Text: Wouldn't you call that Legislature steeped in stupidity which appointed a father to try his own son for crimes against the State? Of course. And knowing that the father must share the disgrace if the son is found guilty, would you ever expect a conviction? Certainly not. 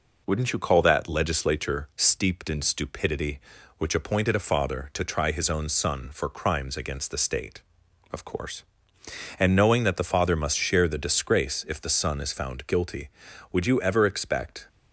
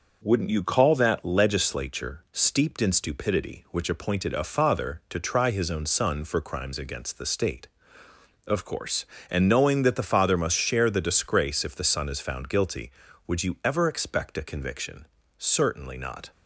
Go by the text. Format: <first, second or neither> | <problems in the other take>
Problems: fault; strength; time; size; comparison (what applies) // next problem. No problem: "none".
second | stops before "a conviction Certainly not"; at 14.6 s